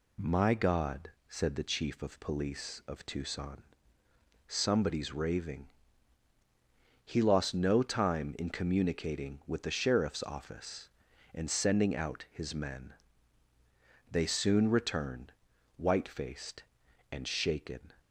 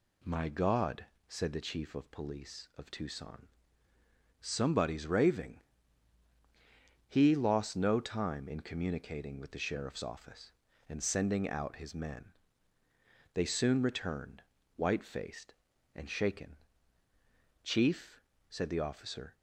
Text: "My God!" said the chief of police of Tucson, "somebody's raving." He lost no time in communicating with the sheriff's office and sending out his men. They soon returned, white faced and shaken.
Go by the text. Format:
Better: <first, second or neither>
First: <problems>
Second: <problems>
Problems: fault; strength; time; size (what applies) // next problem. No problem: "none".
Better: first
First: none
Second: goes on to say "Chief said the officer"; strong; from 17.6 s on; 1.7 s long